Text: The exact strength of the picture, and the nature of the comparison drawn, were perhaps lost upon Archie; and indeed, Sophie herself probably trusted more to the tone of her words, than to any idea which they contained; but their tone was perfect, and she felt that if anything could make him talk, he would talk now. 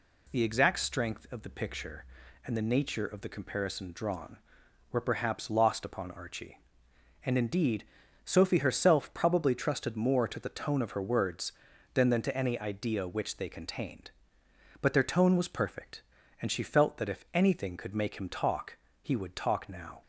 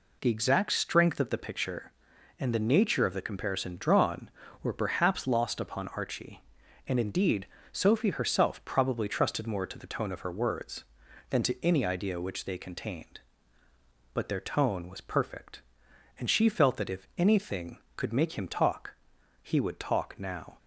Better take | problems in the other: second | says "than" twice; at 12.0 s

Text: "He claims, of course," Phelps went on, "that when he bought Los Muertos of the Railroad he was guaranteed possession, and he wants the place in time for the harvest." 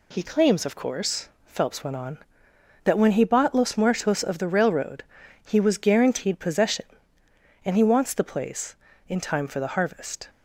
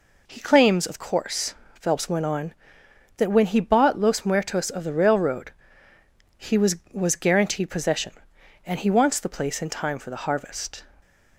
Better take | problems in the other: first | pauses between "Railroad" and "he"; noticeable; at 5.5 s; 0.84 s long; also in the first // says "was" twice; at 6.9 s

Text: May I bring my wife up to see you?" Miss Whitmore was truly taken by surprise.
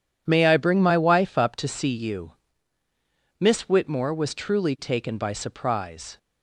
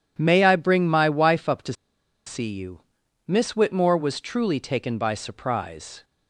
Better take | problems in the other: first | pauses between "to" and "see"; noticeable; at 1.7 s; 0.53 s long

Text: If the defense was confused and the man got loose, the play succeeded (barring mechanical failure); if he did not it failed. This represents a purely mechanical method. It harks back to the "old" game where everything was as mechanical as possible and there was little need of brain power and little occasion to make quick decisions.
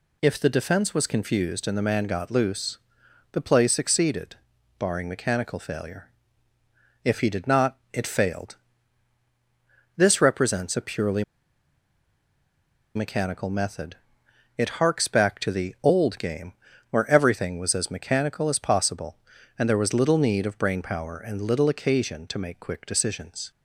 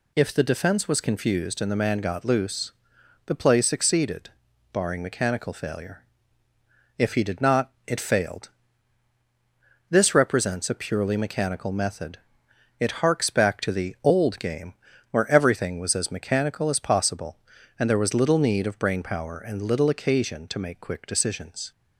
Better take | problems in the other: second | pauses between "not" and "it"; slight; at 7.7 s; 0.16 s long; slight in the second // pauses between "purely" and "mechanical"; strong; at 11.2 s; 1.7 s long // pauses between "game" and "where"; at 16.5 s; 0.38 s long; also in the second

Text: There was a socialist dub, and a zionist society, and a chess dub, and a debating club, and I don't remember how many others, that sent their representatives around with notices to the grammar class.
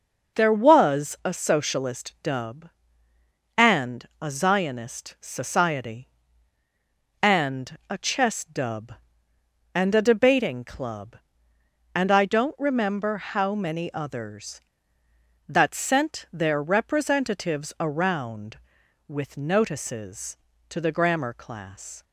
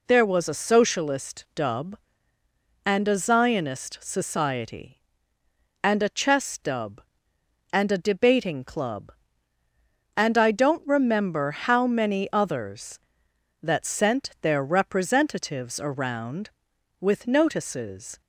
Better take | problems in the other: first | stops before "to the grammar class"; at 18.2 s

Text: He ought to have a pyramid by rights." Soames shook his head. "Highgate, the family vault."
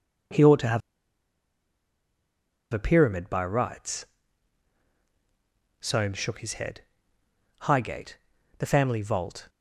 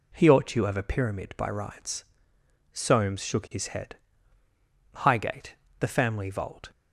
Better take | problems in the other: second | pauses between "have" and "a"; strong; at 0.8 s; 1.9 s long

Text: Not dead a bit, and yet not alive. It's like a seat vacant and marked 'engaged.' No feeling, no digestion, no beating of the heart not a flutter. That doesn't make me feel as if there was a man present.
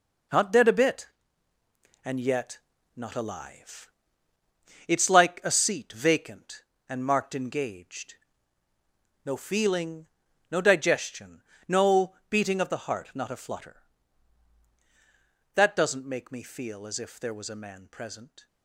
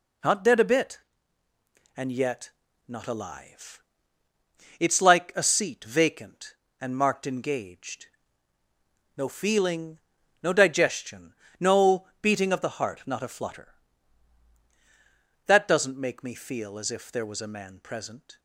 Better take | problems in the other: second | gets quieter; strong; throughout; 8.5 dB // pauses between "yet" and "not"; slight; at 2.5 s; 0.36 s long; slight in the second

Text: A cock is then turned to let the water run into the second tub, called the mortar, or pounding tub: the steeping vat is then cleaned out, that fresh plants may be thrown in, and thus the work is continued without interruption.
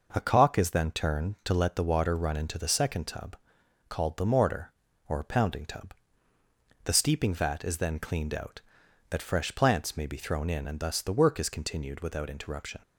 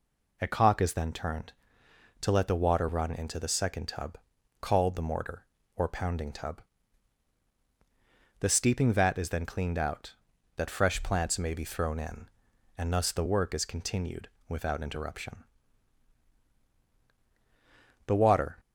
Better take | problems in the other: first | pauses between "continued" and "without"; slight; at 14.2 s; 0.18 s long // goes on to say "The water"; from 18.0 s on; 0.54 s long

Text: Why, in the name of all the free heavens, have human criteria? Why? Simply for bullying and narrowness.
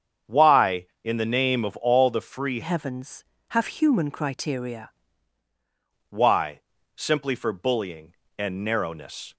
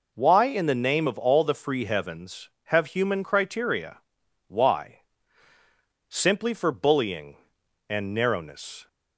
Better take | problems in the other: second | starts louder than the rest; strong; until 1.4 s; 7.5 dB // changes voice from "heavens" to "criteria"; from 2.6 to 4.9 s; 2.3 s long

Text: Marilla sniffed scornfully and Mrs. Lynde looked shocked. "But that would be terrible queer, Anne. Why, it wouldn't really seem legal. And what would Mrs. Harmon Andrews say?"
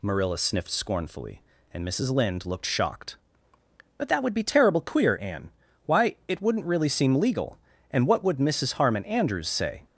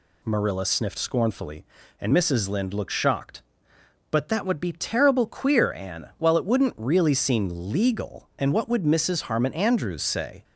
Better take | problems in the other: first | says "While" for "Why"; at 6.1 s

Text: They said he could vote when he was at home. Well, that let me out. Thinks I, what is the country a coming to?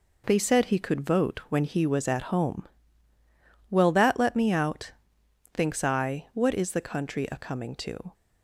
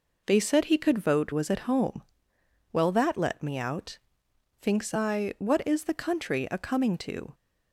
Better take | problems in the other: first | skips "when he"; at 1.3 s

